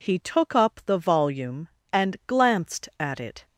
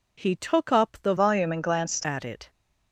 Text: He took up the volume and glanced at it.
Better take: first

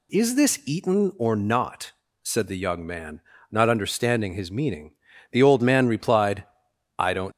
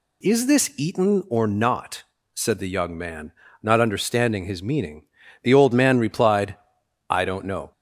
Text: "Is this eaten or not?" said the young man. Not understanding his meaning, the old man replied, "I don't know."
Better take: second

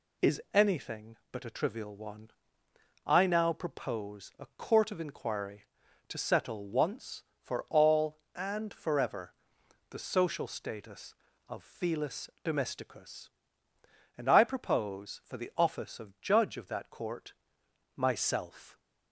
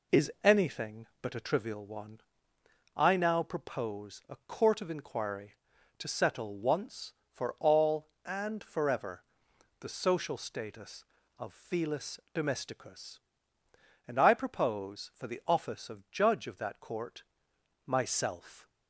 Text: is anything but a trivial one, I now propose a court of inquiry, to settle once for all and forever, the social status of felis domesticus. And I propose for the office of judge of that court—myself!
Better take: first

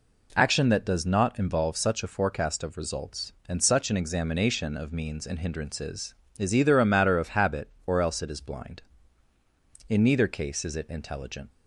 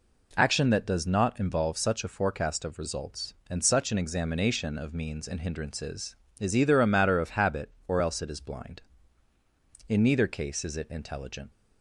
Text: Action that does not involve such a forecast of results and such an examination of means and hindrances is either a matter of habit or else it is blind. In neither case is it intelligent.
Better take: neither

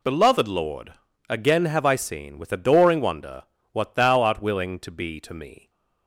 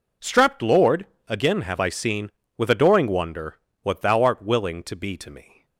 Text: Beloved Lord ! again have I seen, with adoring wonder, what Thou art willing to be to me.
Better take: first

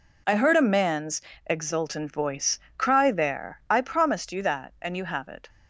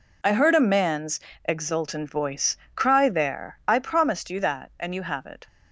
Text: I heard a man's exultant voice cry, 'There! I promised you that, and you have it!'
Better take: neither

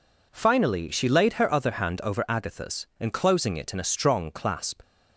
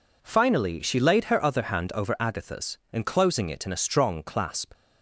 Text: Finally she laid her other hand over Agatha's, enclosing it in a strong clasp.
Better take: neither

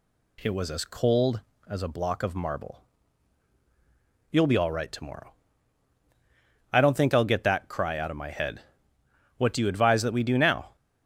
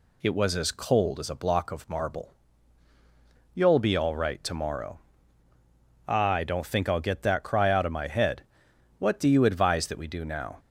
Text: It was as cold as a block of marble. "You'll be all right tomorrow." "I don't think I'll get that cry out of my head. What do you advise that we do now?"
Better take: neither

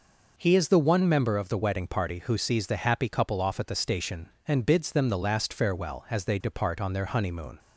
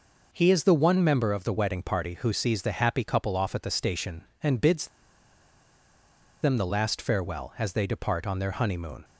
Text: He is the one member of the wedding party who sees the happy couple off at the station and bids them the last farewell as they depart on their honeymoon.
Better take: first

